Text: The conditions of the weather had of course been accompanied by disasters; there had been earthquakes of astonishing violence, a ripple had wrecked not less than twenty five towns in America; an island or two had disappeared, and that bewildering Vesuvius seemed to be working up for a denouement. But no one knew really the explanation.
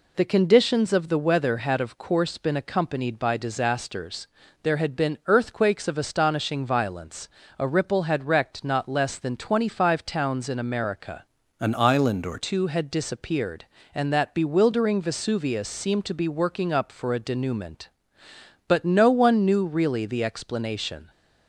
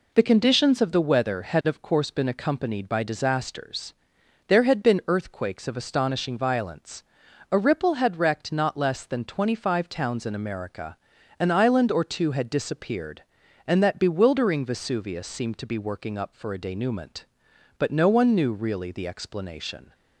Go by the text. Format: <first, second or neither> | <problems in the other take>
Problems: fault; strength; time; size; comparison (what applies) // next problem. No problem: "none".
second | changes voice from "an" to "or"; from 11.5 to 12.3 s; 0.8 s long